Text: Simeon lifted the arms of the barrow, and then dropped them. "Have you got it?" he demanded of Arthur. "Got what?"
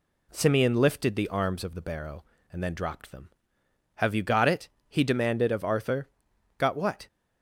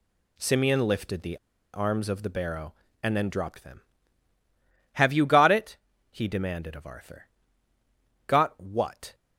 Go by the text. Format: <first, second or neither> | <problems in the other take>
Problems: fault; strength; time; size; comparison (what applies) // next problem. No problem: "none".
first | pauses between "the" and "arms"; at 1.3 s; 0.37 s long